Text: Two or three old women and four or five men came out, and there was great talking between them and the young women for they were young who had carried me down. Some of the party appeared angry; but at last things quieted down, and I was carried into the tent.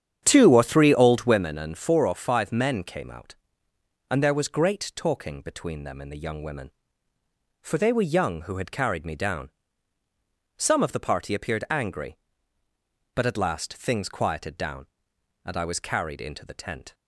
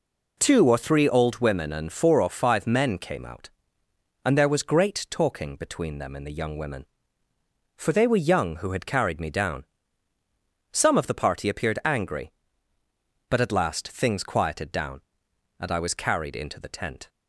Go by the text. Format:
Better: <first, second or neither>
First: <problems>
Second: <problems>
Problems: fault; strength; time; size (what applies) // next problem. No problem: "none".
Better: second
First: starts louder than the rest; strong; until 1.5 s; 9 dB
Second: none